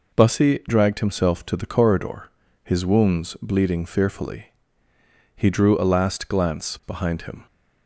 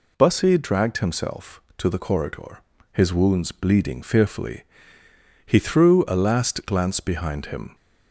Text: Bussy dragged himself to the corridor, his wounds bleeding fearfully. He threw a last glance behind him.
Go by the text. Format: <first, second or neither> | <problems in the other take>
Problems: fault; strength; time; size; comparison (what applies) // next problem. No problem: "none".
second | says "drew" for "threw"; at 5.4 s